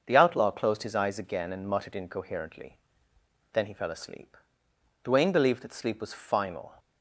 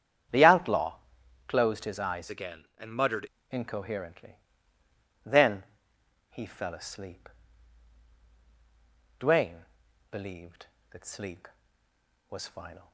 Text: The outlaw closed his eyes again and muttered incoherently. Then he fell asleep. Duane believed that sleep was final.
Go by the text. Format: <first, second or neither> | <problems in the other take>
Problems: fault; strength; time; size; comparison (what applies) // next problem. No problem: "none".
first | starts louder than the rest; strong; until 1.8 s; 8.5 dB; also in the first // pauses between "outlaw" and "closed"; noticeable; at 0.9 s; 0.52 s long // changes voice from "again" to "muttered"; from 2.2 to 3.2 s; 1.0 s long // pauses between "Then" and "he"; noticeable; at 5.6 s; 0.66 s long // pauses between "Duane" and "believed"; noticeable; at 9.6 s; 0.48 s long